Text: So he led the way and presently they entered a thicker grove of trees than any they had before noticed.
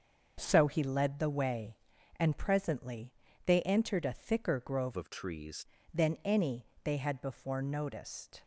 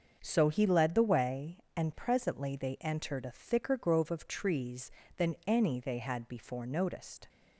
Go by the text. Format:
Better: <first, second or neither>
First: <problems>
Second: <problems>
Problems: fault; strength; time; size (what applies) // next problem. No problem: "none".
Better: second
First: starts louder than the rest; until 1.3 s; 6.5 dB // pauses between "presently" and "they"; slight; at 3.1 s; 0.32 s long // changes voice from "of" to "trees"; from 4.9 to 5.6 s; 0.7 s long // pauses between "any" and "they"; slight; at 6.6 s; 0.18 s long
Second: starts louder than the rest; until 1.2 s; 6.5 dB